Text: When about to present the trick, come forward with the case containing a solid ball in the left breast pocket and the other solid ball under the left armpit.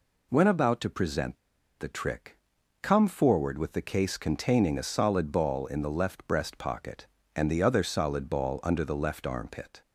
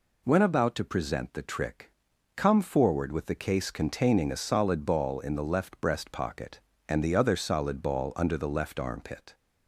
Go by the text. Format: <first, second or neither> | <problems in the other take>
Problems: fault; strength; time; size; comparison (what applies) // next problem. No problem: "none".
second | pauses between "present" and "the"; at 1.3 s; 0.41 s long